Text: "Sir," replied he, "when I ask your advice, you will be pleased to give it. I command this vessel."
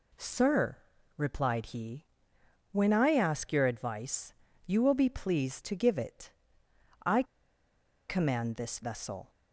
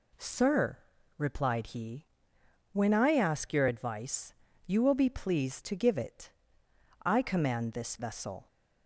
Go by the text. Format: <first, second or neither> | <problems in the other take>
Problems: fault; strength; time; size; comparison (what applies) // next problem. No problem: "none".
second | pauses between "I" and "command"; noticeable; at 7.2 s; 0.85 s long